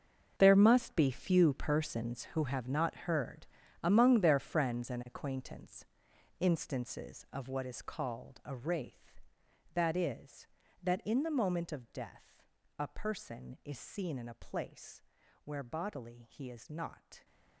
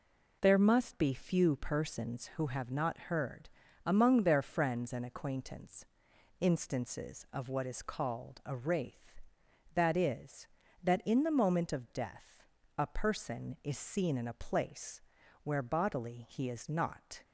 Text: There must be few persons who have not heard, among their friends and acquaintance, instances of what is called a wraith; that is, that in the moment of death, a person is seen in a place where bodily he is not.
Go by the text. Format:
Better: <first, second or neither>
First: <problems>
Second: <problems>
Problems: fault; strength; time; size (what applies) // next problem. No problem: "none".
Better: second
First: gets quieter; strong; throughout; 14.5 dB // pauses between "place" and "where"; at 15.0 s; 0.42 s long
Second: pauses between "place" and "where"; at 14.9 s; 0.42 s long